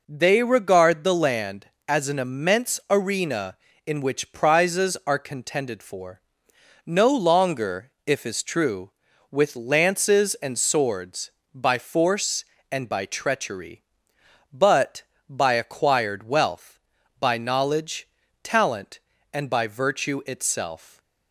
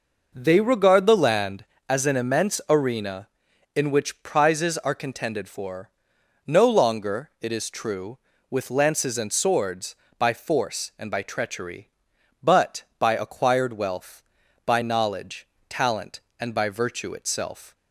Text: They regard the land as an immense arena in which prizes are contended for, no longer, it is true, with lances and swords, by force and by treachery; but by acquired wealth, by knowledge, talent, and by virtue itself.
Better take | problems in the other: second | says "if" for "it"; at 8.0 s

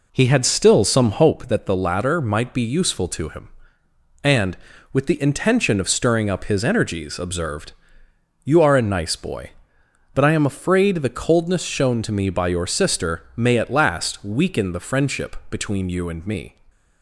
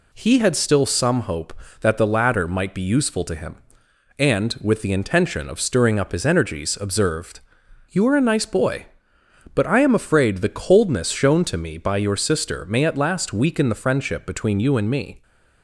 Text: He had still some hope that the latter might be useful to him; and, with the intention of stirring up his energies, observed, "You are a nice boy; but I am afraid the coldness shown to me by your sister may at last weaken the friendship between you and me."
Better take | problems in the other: second | starts louder than the rest; until 1.3 s; 3.5 dB

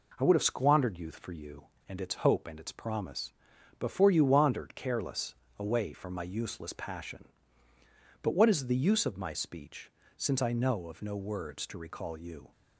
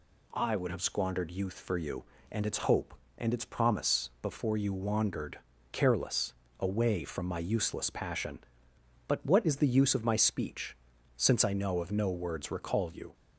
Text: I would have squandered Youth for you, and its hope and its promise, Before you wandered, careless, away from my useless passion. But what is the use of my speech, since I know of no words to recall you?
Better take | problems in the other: first | skips "to"; at 12.5 s

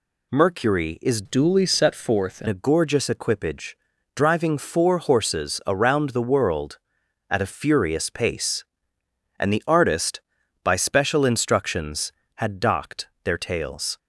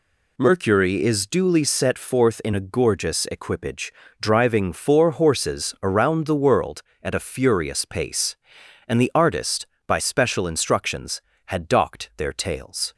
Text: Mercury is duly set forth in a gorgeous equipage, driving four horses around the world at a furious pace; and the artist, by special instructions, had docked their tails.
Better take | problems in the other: second | changes voice from "duly" to "in"; from 1.2 to 2.4 s; 1.2 s long // pauses between "docked" and "their"; slight; at 13.0 s; 0.16 s long

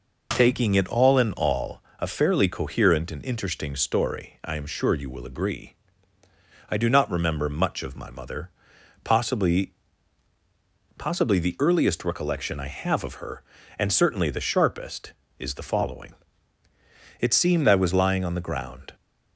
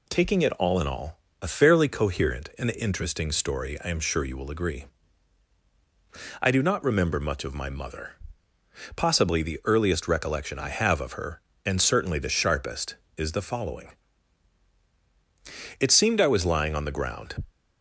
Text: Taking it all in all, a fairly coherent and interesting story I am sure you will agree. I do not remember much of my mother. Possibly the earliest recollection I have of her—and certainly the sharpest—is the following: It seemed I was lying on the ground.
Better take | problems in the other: second | says "Possibly" twice; at 10.9 s

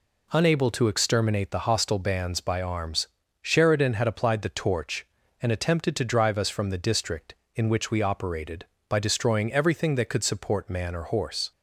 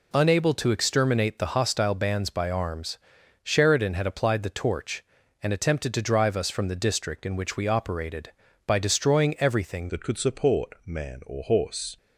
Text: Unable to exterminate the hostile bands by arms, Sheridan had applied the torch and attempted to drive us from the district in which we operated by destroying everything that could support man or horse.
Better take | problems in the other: first | changes voice at "that"; from 9.8 s on; 2.1 s long

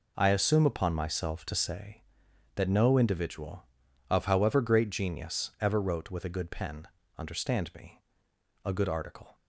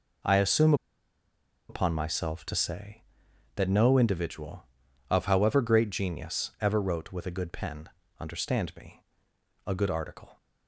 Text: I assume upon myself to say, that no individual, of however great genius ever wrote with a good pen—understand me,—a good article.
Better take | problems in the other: first | pauses between "assume" and "upon"; noticeable; at 0.7 s; 0.94 s long

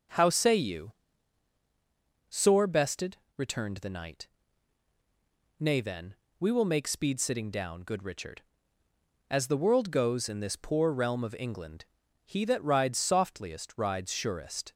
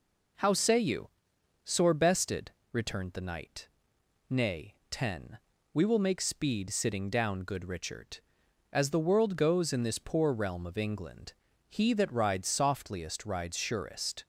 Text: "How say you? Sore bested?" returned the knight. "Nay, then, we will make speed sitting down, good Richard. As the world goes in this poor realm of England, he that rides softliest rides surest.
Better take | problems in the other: first | says "ten" for "then"; at 4.9 s

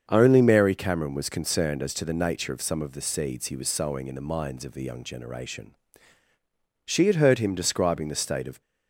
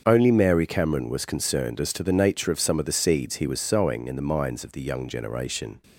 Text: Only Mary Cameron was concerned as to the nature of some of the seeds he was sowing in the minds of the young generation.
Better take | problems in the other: second | starts louder than the rest; until 1.0 s; 7 dB; also in the second // goes on to say "She had heard him describing the state of"; strong; from 6.8 s on; 1.7 s long

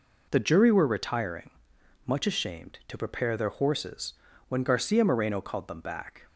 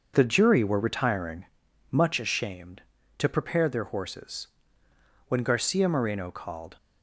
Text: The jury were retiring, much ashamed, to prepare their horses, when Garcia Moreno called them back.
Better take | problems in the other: first | starts louder than the rest; noticeable; until 1.1 s; 6 dB // stops before "them back"; at 6.7 s

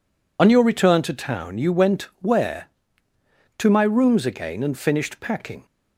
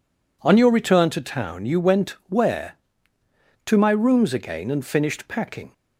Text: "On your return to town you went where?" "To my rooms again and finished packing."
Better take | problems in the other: second | loses the start of "On"; at 0.3 s; 65 ms // pauses between "went" and "where"; slight; at 2.0 s; 0.18 s long; slight in the second

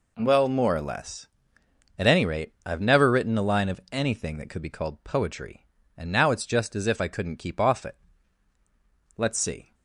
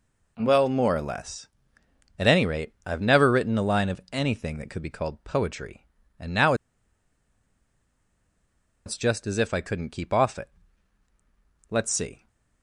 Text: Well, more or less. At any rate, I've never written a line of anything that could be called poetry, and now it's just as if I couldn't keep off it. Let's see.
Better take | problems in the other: first | pauses between "now" and "it's"; strong; at 6.5 s; 2.3 s long

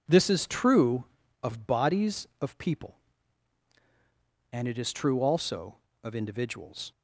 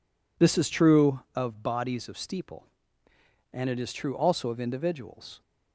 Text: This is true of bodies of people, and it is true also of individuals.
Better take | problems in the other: first | says "steeple" for "people"; at 2.1 s

